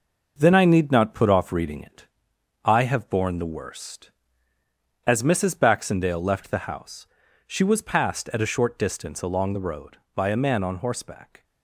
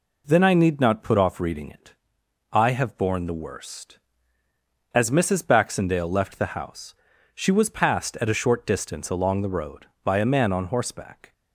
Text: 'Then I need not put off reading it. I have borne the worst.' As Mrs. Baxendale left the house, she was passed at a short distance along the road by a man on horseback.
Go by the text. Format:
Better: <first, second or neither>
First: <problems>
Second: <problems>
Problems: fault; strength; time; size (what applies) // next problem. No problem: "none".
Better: second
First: gets quieter; noticeable; throughout; 5 dB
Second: none